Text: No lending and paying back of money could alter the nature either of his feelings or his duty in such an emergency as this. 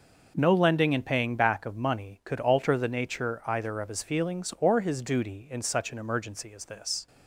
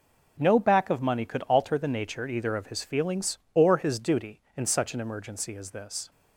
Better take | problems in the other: first | skips "lending and paying"; at 0.6 s

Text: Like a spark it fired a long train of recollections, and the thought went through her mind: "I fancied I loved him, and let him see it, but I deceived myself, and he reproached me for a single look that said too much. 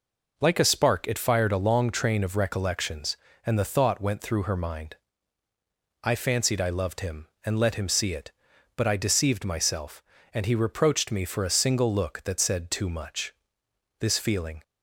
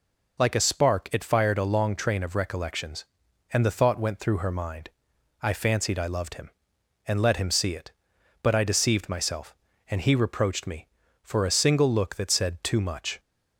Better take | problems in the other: second | goes on to say "This feeling"; noticeable; from 13.9 s on; 0.64 s long

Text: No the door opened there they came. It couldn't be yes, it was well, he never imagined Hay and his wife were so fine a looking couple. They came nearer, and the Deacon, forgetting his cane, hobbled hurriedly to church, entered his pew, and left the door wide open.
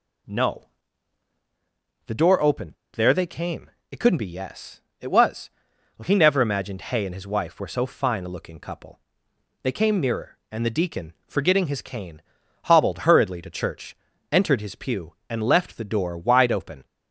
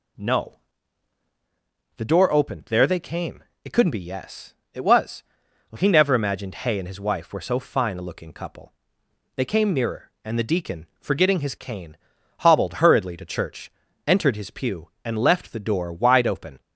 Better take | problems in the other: second | pauses between "No" and "the"; strong; at 0.6 s; 1.4 s long; strong in the second // pauses between "opened" and "there"; slight; at 2.7 s; 0.21 s long // pauses between "was" and "well"; noticeable; at 5.4 s; 0.48 s long; noticeable in the second

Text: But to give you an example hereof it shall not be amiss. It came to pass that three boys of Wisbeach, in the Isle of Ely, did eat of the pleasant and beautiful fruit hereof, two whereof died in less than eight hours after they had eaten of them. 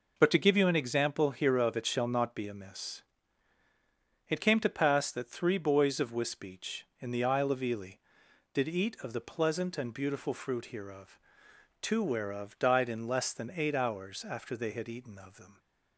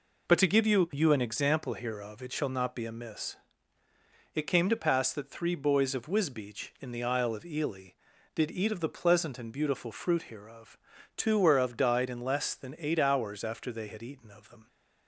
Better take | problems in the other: first | says "you" twice; at 0.9 s

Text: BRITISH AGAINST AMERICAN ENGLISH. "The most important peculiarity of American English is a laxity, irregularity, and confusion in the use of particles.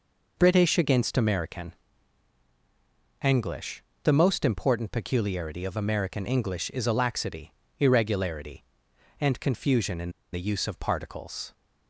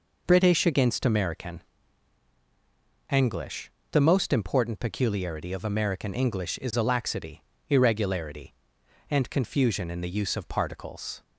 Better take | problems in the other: second | pauses between "AMERICAN" and "ENGLISH"; strong; at 1.7 s; 1.5 s long; strong in the second // pauses between "in" and "the"; slight; at 10.1 s; 0.21 s long

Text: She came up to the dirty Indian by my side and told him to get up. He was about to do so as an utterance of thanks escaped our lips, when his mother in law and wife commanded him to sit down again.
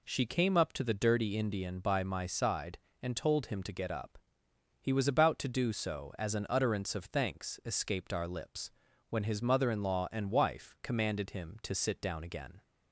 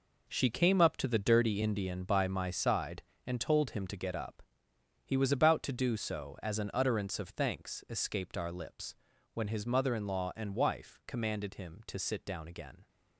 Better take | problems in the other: first | gets quieter; strong; throughout; 10 dB

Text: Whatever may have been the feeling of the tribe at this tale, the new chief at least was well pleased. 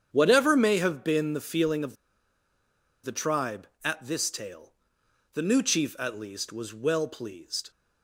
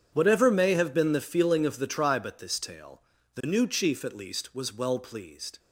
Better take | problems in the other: second | starts louder than the rest; strong; until 1.1 s; 8.5 dB; strong in the second // pauses between "of" and "the"; at 1.9 s; 1.0 s long

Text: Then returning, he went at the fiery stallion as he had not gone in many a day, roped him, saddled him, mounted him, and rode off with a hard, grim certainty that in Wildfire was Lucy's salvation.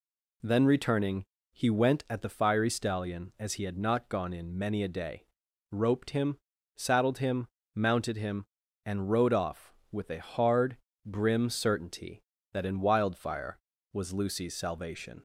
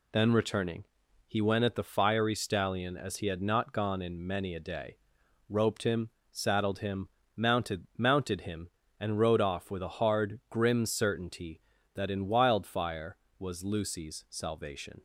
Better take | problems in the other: first | says "mounted" twice; at 7.9 s

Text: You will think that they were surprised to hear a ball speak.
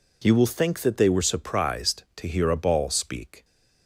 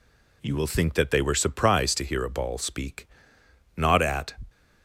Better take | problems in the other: first | goes on to say "Not at"; noticeable; from 3.7 s on; 0.64 s long

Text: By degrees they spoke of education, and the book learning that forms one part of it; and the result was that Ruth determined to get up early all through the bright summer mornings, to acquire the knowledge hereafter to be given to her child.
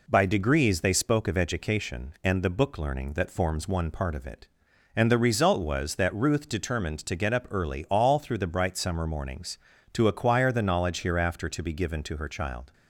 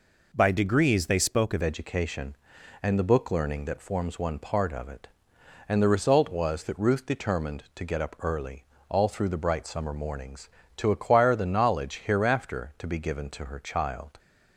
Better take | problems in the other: first | changes voice at "education"; from 1.6 s on; 12.5 s long // pauses between "early" and "all"; slight; at 8.6 s; 0.24 s long

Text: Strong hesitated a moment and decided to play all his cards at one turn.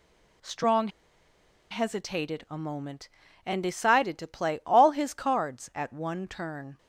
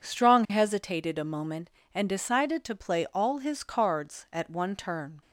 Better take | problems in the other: second | pauses between "Strong" and "hesitated"; noticeable; at 0.8 s; 0.82 s long

